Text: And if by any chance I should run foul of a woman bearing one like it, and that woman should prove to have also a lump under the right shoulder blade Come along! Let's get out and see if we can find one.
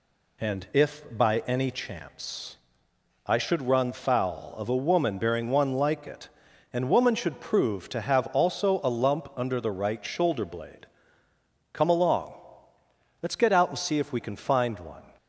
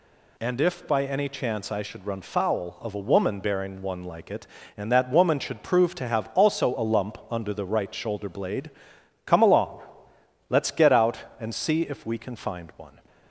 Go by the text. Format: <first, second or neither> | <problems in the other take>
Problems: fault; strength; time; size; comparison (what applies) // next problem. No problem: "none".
second | pauses between "chance" and "I"; noticeable; at 2.5 s; 0.70 s long // skips "that"; at 6.8 s // pauses between "blade" and "Come"; noticeable; at 10.8 s; 0.86 s long; noticeable in the second